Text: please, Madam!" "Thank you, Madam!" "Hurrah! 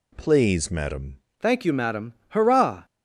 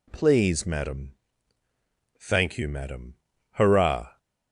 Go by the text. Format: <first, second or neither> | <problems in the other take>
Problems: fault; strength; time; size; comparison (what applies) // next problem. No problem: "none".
second | changes voice at "Thank"; from 1.4 s on; 1.4 s long